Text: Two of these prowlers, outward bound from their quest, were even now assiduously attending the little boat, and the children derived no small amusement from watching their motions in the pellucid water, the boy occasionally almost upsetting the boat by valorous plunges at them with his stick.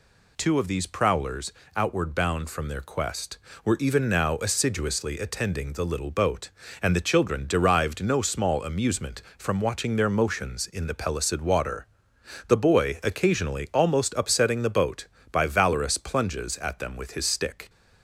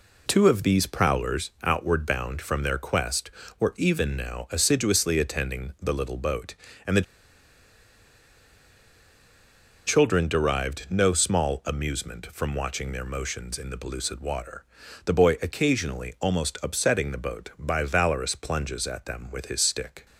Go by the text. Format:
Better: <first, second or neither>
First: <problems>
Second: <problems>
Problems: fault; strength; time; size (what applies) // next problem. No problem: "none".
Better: first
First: none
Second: pauses between "the" and "children"; strong; at 7.0 s; 2.8 s long